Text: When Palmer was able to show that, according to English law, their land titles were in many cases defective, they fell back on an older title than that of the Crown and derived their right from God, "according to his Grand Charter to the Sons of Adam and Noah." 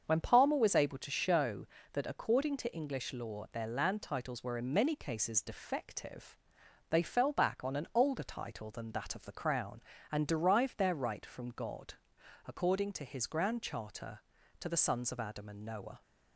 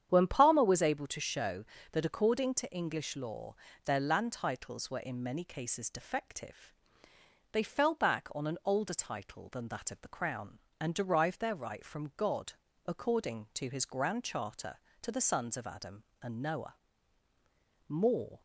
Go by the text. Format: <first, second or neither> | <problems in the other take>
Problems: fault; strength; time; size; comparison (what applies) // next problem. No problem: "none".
first | starts louder than the rest; strong; until 1.1 s; 9 dB; also in the first // goes on to say "More"; from 17.8 s on; 0.54 s long